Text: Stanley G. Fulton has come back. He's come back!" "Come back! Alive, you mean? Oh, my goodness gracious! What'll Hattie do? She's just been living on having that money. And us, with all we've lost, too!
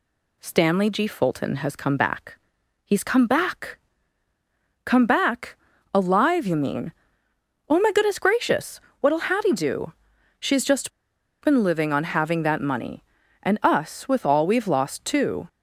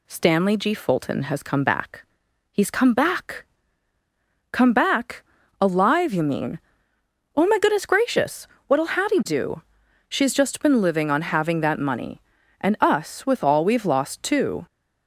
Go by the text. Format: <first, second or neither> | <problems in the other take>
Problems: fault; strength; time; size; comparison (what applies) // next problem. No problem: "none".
second | pauses between "just" and "been"; noticeable; at 10.9 s; 0.54 s long